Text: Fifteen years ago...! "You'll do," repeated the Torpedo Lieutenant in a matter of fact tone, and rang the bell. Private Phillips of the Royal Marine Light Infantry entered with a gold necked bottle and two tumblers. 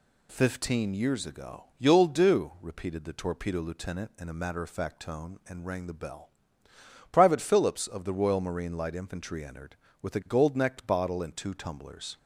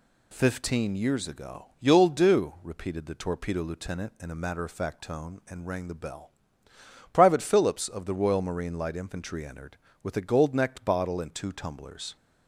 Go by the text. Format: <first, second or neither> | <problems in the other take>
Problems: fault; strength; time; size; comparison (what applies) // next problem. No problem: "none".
neither | none